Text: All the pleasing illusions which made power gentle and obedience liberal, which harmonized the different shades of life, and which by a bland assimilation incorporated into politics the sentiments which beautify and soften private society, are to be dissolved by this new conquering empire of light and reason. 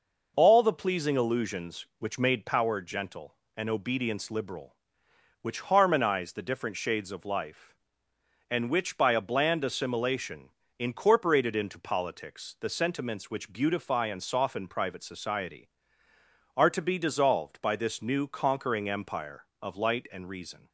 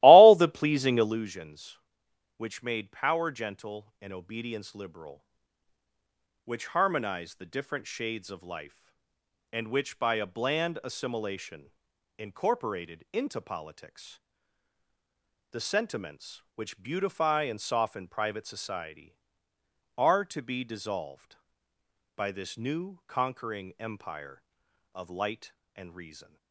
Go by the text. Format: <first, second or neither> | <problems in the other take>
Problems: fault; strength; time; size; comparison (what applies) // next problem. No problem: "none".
first | starts louder than the rest; strong; until 1.2 s; 17 dB // pauses between "assimilation" and "incorporated"; noticeable; at 11.7 s; 0.48 s long; slight in the first // pauses between "politics" and "the"; strong; at 14.1 s; 1.3 s long